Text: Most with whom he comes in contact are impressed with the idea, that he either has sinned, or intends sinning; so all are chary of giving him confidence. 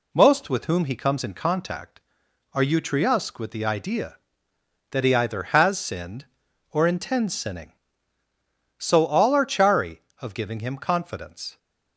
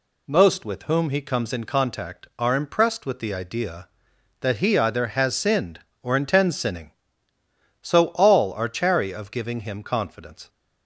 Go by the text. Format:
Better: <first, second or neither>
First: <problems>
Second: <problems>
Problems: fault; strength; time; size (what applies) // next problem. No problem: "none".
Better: second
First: says "utriusque" for "impressed"; at 2.6 s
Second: none